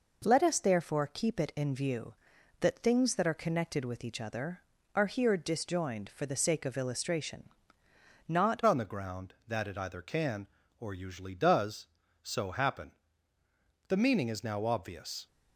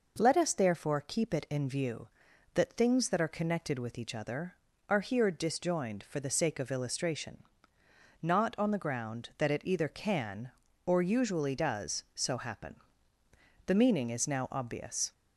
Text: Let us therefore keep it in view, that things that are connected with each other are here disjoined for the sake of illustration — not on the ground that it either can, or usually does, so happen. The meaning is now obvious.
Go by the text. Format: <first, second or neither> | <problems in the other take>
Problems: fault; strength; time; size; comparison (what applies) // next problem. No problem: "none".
second | changes voice at "on"; from 8.6 s on; 6.6 s long